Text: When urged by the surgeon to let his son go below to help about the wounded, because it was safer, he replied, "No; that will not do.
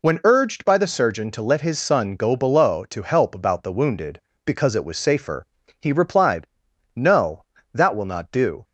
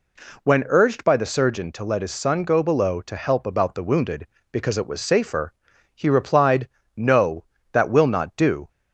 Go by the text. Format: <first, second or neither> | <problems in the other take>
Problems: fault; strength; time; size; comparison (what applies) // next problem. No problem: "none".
neither | none